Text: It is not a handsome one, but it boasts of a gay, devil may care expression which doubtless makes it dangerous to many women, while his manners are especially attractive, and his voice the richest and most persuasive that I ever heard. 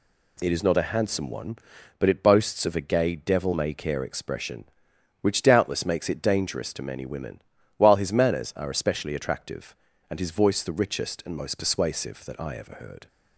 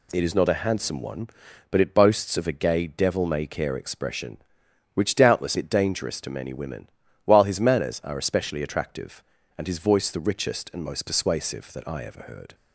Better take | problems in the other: first | skips "makes"; at 5.5 s

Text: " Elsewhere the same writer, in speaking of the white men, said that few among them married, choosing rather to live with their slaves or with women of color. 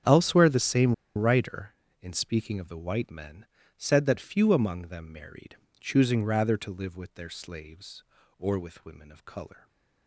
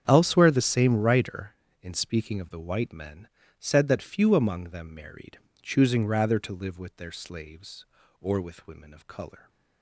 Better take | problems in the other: second | starts louder than the rest; strong; until 1.2 s; 8 dB; strong in the second // pauses between "same" and "writer"; slight; at 0.9 s; 0.23 s long

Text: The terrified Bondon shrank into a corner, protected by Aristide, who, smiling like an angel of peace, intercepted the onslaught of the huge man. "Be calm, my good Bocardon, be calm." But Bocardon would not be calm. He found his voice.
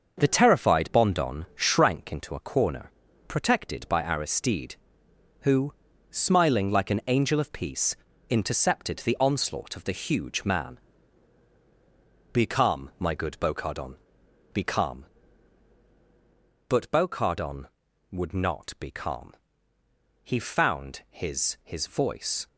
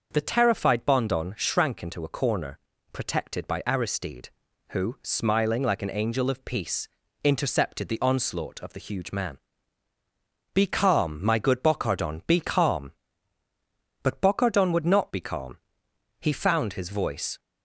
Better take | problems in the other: second | starts louder than the rest; until 1.2 s; 6.5 dB; noticeable in the second // says "his" twice; at 21.6 s

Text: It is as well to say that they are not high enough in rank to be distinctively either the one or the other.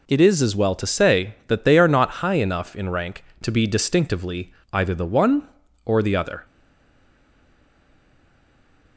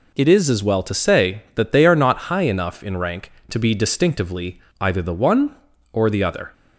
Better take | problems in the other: second | pauses between "distinctively" and "either"; slight; at 4.5 s; 0.18 s long; slight in the second // stays silent after the last word; from 6.4 s on; 2.5 s long

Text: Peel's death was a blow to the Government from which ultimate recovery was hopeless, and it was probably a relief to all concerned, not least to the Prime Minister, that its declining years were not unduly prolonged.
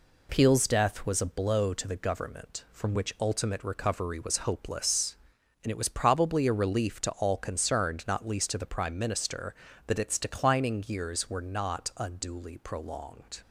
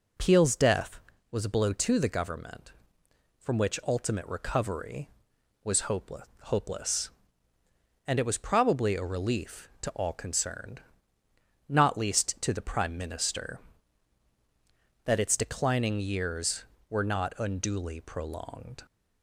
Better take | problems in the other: first | says "hopeless" twice; at 6.4 s

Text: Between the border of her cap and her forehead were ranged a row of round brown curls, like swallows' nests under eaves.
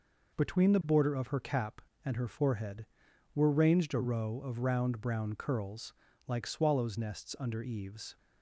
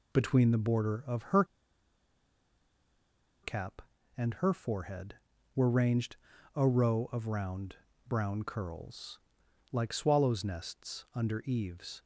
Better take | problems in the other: first | pauses between "her" and "cap"; strong; at 1.4 s; 1.9 s long // pauses between "ranged" and "a"; at 6.1 s; 0.40 s long // pauses between "round" and "brown"; slight; at 7.7 s; 0.32 s long

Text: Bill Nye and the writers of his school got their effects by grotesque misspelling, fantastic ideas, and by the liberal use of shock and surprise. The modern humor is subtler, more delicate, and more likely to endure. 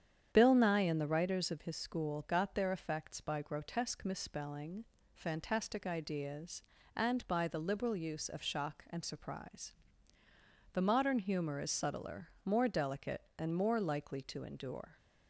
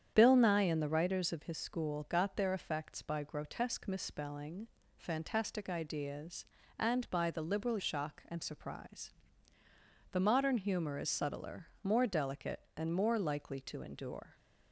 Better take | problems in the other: first | starts louder than the rest; strong; until 1.1 s; 9 dB; strong in the first // skips "use of"; at 7.7 s

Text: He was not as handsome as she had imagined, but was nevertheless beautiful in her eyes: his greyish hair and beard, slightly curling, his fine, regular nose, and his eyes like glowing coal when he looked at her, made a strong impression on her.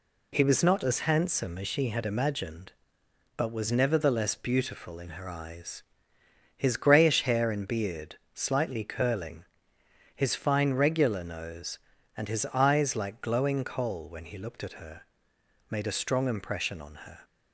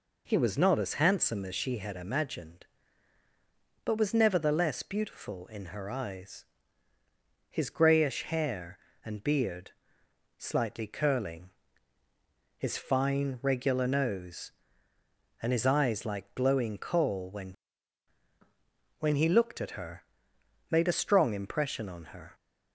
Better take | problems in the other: first | says "when" twice; at 19.0 s

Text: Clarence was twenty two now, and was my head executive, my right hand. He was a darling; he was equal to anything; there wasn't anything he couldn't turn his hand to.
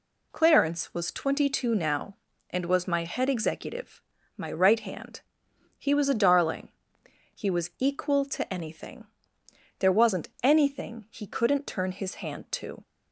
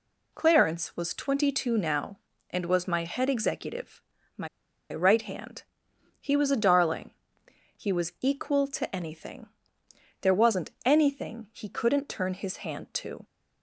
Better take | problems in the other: first | pauses between "my" and "right"; at 4.4 s; 0.44 s long

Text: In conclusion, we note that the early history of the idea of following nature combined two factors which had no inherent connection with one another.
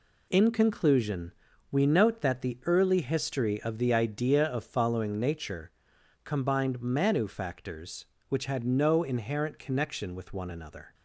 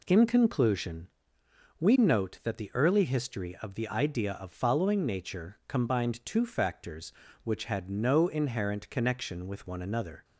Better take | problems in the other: second | pauses between "nature" and "combined"; noticeable; at 5.7 s; 0.52 s long // says "manu" for "two"; at 6.7 s

